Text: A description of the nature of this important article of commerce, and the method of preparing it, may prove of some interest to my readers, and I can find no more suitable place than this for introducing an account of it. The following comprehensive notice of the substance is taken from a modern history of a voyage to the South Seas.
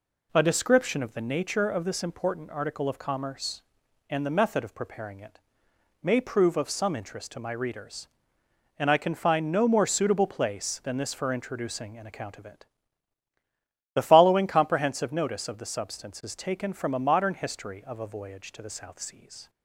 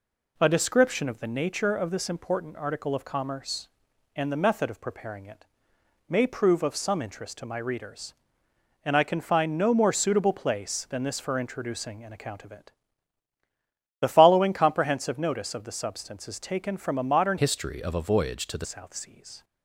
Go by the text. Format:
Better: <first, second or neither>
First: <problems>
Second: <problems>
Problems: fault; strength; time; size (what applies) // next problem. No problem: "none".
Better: first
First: none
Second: changes voice from "history" to "the"; from 17.3 to 18.6 s; 1.3 s long